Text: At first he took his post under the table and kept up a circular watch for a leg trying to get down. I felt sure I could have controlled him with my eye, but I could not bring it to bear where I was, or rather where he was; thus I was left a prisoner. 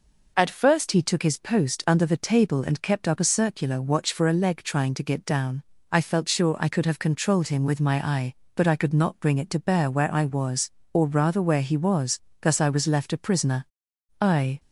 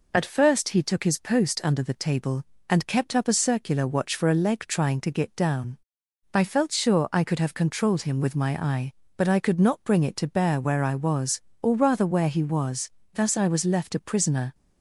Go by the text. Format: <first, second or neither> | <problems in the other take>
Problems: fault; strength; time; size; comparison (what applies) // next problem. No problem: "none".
second | goes on to say "I"; slight; from 14.1 s on; 0.40 s long